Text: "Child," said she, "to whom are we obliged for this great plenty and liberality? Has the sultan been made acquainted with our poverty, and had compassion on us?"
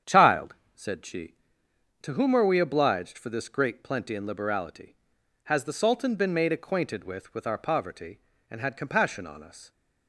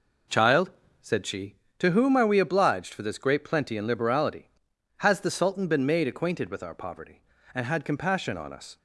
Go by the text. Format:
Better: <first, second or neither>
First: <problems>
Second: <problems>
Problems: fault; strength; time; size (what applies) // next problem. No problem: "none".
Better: second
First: starts louder than the rest; strong; until 1.2 s; 8.5 dB // says "with" twice; at 7.3 s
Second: none